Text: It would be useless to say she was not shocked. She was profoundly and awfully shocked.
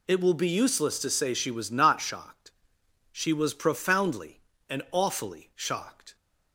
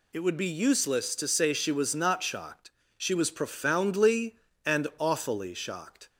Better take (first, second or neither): second